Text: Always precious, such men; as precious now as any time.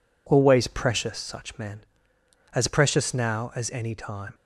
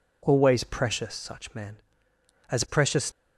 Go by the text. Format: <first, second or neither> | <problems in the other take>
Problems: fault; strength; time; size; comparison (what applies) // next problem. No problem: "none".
first | stops before "now as any time"; at 3.1 s